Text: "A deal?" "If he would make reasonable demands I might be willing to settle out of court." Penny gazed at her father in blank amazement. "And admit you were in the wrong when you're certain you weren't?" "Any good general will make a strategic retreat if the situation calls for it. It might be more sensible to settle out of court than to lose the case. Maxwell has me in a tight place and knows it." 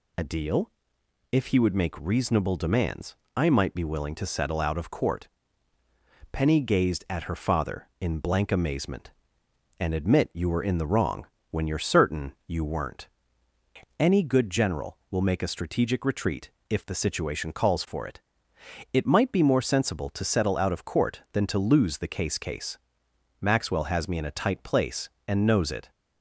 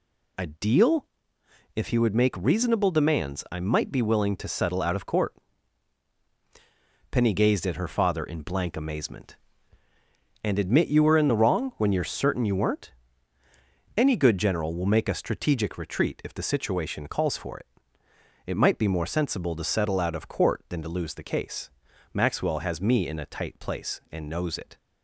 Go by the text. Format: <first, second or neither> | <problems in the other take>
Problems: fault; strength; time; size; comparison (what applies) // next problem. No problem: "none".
second | pauses between "demands" and "I"; slight; at 3.1 s; 0.18 s long // pauses between "wrong" and "when"; slight; at 11.2 s; 0.24 s long // pauses between "retreat" and "if"; slight; at 16.5 s; 0.18 s long // says "case" twice; at 22.3 s